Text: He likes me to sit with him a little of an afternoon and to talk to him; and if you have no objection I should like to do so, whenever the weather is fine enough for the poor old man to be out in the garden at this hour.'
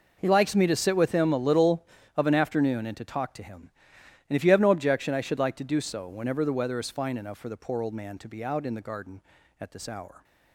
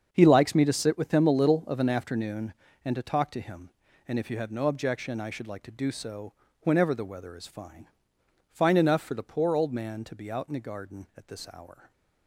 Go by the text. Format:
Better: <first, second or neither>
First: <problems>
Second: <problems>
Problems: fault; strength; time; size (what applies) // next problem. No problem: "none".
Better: first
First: none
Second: starts louder than the rest; until 1.1 s; 7 dB // says "fine" twice; at 8.5 s // stays silent after the last word; slight; from 11.7 s on; 0.5 s long